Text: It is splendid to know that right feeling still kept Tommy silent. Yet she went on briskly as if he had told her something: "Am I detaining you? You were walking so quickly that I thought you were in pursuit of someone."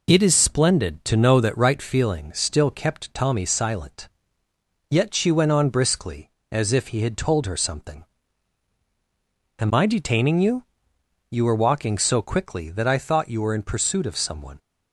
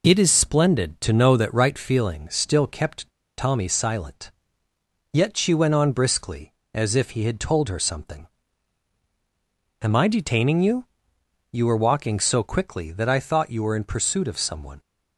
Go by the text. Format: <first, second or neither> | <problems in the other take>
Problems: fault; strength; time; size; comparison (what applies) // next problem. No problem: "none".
first | pauses between "kept" and "Tommy"; slight; at 3.0 s; 0.27 s long